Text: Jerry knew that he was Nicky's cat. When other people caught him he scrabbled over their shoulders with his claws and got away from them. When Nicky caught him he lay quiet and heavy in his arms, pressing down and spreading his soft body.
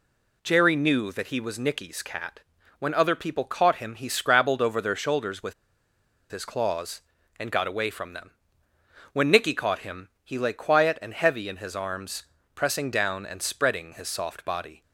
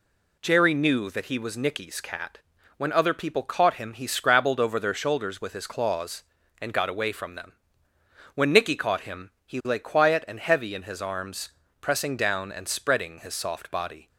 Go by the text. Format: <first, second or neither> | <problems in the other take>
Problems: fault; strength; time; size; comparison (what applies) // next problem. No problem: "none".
second | pauses between "with" and "his"; noticeable; at 5.5 s; 0.76 s long